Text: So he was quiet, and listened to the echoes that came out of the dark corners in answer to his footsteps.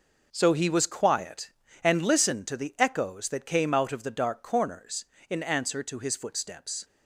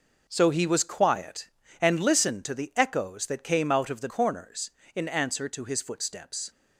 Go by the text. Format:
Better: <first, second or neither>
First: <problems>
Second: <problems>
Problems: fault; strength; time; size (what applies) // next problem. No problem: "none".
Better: first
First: none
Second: skips "dark"; at 4.0 s